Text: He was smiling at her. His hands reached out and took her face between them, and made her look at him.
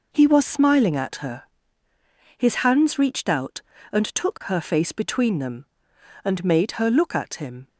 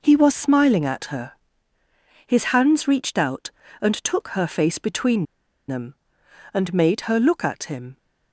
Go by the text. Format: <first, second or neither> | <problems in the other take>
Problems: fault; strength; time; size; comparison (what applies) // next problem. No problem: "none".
first | pauses between "between" and "them"; at 5.2 s; 0.43 s long